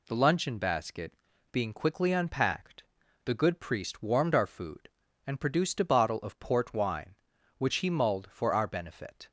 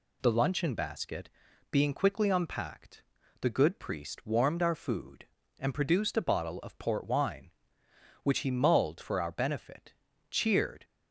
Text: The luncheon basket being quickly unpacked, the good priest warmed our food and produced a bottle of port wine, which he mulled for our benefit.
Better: first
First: pauses between "basket" and "being"; at 1.1 s; 0.40 s long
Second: pauses between "basket" and "being"; at 1.3 s; 0.40 s long // goes on to say "Cheered"; from 10.3 s on; 0.54 s long

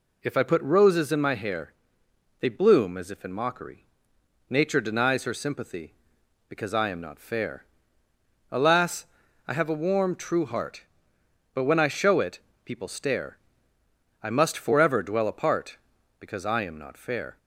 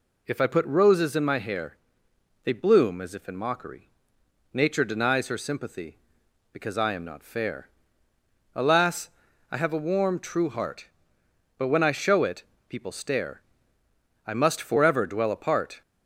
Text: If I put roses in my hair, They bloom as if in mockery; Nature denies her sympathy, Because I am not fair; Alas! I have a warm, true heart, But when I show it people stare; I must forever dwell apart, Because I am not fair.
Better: first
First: pauses between "it" and "people"; slight; at 12.3 s; 0.28 s long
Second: pauses between "it" and "people"; slight; at 12.4 s; 0.28 s long // stops before "Because I am not fair"; at 15.8 s

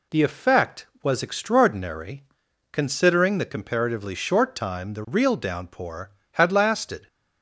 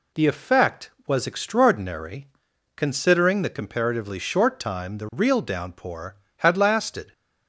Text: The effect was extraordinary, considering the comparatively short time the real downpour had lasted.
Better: neither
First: none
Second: none

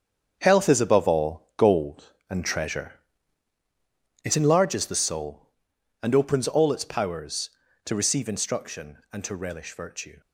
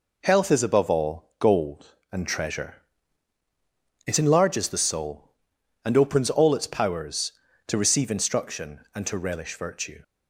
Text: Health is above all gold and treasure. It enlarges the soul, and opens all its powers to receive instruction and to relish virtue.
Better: second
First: gets quieter; strong; throughout; 8.5 dB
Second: none

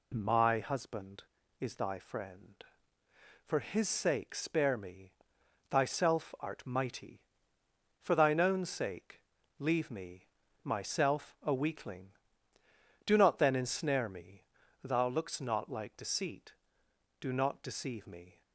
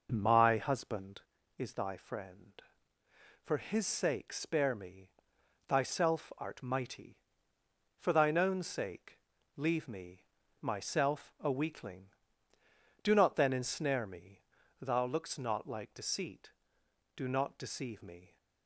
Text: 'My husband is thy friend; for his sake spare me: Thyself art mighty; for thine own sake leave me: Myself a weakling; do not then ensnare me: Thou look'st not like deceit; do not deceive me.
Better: first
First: pauses between "sake" and "leave"; slight; at 9.2 s; 0.36 s long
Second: starts louder than the rest; noticeable; until 1.3 s; 5.5 dB // pauses between "sake" and "leave"; slight; at 9.1 s; 0.36 s long

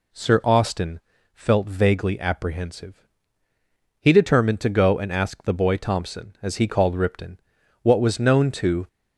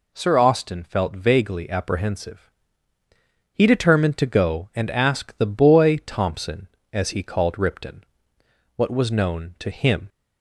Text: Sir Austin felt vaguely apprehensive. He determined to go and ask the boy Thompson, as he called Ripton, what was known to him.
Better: second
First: pauses between "Austin" and "felt"; slight; at 0.9 s; 0.34 s long // stops before "him"; at 8.8 s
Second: none

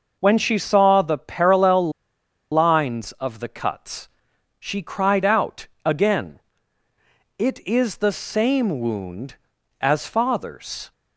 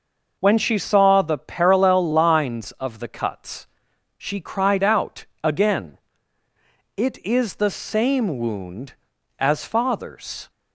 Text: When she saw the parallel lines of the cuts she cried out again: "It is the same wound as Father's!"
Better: second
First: pauses between "parallel" and "lines"; noticeable; at 1.9 s; 0.59 s long // pauses between "cuts" and "she"; noticeable; at 4.0 s; 0.50 s long // pauses between "out" and "again"; slight; at 5.6 s; 0.18 s long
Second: pauses between "cuts" and "she"; noticeable; at 3.6 s; 0.50 s long // pauses between "out" and "again"; slight; at 5.2 s; 0.18 s long

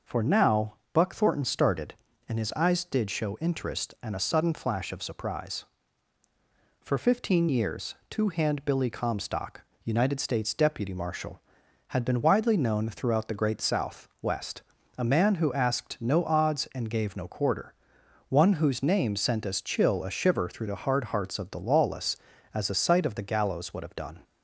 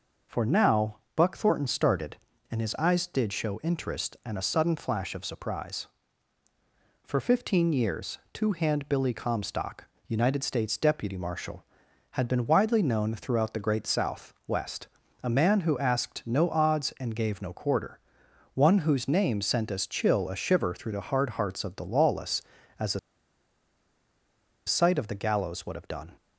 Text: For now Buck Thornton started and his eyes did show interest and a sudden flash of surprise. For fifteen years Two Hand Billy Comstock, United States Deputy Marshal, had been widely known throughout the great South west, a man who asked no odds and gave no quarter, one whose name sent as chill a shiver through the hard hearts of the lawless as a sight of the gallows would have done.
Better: first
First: pauses between "now" and "Buck"; slight; at 0.7 s; 0.18 s long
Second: pauses between "now" and "Buck"; slight; at 0.9 s; 0.18 s long // pauses between "a" and "sight"; strong; at 22.9 s; 1.6 s long

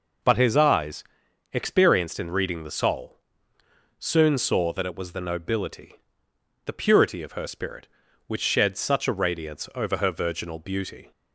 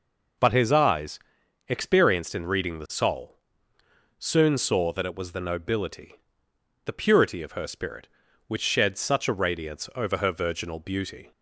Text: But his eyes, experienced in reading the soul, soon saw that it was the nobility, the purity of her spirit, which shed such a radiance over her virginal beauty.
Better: neither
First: none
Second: none

